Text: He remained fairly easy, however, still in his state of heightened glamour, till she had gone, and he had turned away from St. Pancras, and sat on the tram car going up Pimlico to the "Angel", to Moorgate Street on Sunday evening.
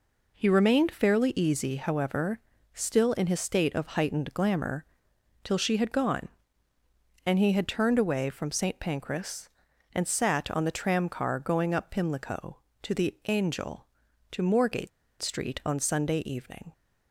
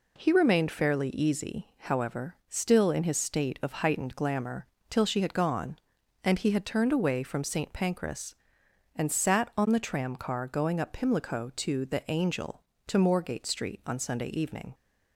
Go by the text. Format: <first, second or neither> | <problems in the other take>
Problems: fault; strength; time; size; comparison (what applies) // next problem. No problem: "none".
second | pauses between "Moorgate" and "Street"; slight; at 14.8 s; 0.32 s long